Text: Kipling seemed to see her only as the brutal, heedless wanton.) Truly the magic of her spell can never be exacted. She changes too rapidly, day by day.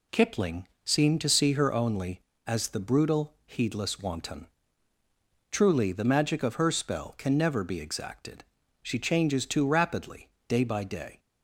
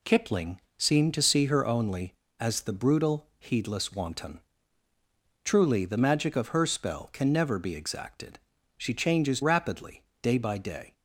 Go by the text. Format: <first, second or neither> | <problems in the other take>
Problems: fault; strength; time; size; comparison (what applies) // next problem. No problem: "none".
first | pauses between "Kipling" and "seemed"; slight; at 0.5 s; 0.18 s long; slight in the first // skips "too"; at 9.4 s